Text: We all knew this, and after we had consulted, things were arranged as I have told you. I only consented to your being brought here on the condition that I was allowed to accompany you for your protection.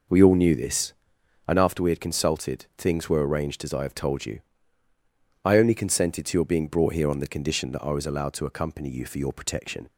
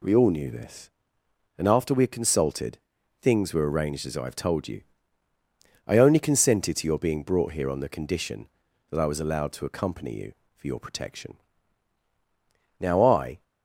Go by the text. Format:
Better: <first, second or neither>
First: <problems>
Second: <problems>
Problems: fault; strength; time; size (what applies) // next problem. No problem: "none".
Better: first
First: none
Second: goes on to say "Now I"; noticeable; from 12.8 s on; 0.62 s long